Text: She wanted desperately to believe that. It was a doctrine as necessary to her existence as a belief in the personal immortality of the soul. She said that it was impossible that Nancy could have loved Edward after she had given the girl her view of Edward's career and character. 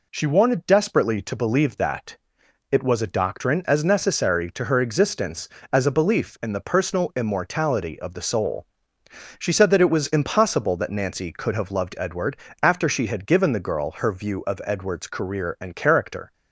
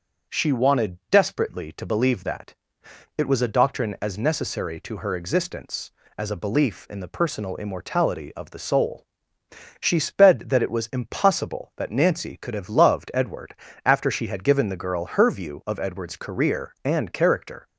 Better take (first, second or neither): first